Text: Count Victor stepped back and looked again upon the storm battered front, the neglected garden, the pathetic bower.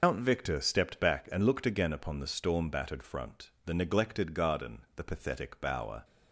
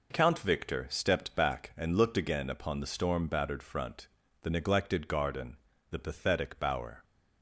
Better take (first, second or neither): second